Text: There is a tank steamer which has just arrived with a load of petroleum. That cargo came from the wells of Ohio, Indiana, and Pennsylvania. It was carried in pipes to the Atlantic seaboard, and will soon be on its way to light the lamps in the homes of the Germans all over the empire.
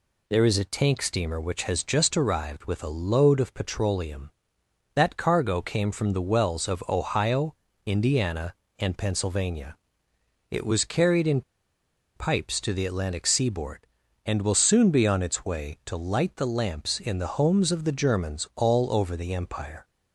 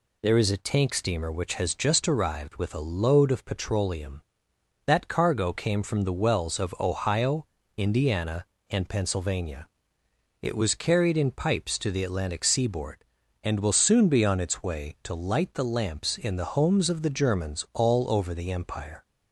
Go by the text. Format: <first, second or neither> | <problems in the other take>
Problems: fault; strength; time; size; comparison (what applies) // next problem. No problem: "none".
second | pauses between "in" and "pipes"; noticeable; at 11.4 s; 0.73 s long